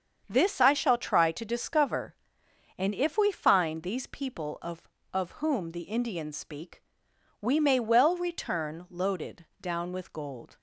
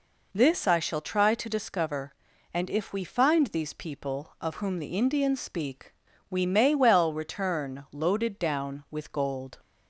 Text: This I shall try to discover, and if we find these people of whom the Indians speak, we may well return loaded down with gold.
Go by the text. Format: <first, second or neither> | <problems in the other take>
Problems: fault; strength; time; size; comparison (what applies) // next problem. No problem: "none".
second | starts louder than the rest; strong; until 1.2 s; 7 dB // says "of" twice; at 5.1 s // pauses between "loaded" and "down"; slight; at 9.4 s; 0.16 s long